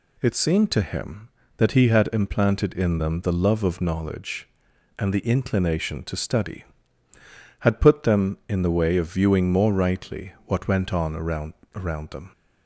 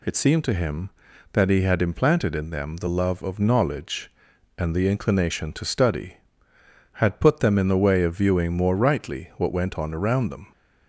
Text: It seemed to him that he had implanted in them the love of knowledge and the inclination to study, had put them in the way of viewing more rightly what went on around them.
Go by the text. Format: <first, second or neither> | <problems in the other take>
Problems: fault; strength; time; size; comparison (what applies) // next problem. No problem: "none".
second | says "around" twice; at 11.7 s